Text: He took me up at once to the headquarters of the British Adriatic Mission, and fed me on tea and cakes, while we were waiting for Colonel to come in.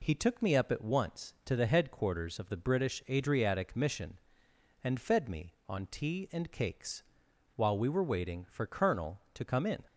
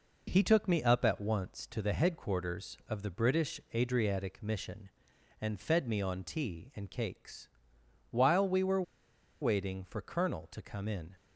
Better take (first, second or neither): first